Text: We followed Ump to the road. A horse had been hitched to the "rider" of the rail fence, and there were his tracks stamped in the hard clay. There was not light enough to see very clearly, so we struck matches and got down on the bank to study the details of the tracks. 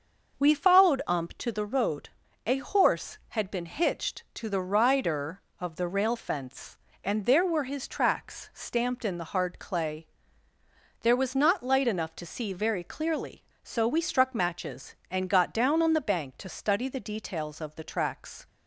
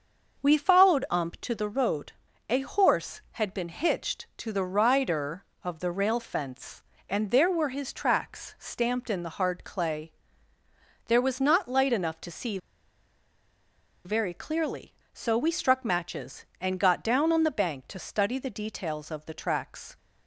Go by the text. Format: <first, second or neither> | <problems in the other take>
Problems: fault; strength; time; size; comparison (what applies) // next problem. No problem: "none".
first | starts louder than the rest; until 1.4 s; 6 dB; also in the first // pauses between "see" and "very"; strong; at 12.5 s; 1.4 s long